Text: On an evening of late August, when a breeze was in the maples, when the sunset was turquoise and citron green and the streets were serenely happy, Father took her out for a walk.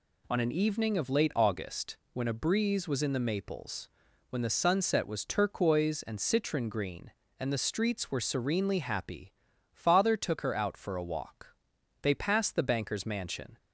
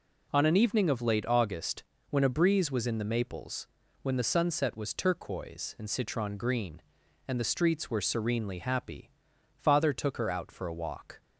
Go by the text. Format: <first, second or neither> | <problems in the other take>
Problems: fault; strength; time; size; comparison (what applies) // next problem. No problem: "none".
second | goes on to say "They passed the banker's mansion"; from 12.0 s on; 1.5 s long